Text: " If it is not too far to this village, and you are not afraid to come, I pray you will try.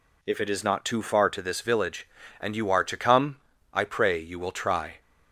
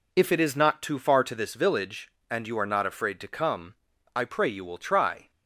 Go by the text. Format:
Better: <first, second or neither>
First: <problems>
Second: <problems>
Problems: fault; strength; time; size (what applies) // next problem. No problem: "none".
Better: second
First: skips "not afraid"; at 2.8 s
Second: none